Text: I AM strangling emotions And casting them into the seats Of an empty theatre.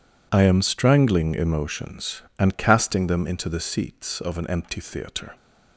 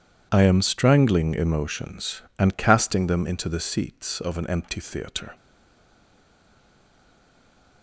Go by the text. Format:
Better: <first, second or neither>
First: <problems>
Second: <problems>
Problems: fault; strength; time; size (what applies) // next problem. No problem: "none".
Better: first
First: none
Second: stays silent after the last word; from 5.3 s on; 2.5 s long